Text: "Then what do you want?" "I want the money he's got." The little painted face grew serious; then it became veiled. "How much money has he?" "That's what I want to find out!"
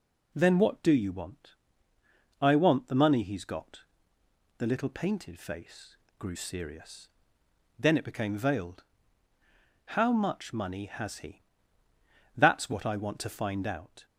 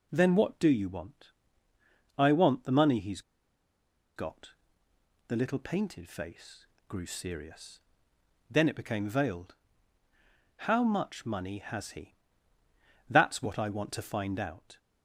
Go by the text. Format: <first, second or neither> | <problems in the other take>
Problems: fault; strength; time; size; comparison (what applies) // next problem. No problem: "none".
first | pauses between "he's" and "got"; noticeable; at 3.2 s; 0.95 s long // pauses between "face" and "grew"; slight; at 6.6 s; 0.22 s long; slight in the first